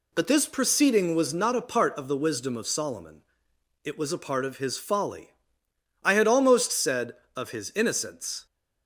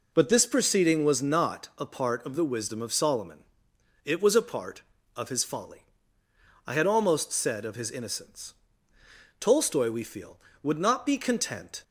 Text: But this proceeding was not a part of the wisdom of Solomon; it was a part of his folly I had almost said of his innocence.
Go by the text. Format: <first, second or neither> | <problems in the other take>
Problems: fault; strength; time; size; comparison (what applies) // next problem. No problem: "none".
first | pauses between "folly" and "I"; noticeable; at 5.8 s; 0.82 s long; noticeable in the first // goes on to say "Tolstoy we feel would not be content"; strong; from 9.3 s on; 2.4 s long